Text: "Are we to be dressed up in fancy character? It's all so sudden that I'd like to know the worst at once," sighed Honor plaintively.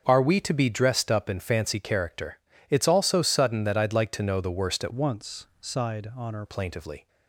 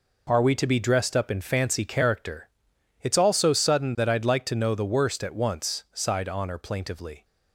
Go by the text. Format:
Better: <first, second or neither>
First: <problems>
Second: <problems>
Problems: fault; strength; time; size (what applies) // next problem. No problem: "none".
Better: second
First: starts louder than the rest; until 1.0 s; 6.5 dB // changes voice from "once" to "Honor"; from 4.9 to 6.4 s; 1.5 s long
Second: none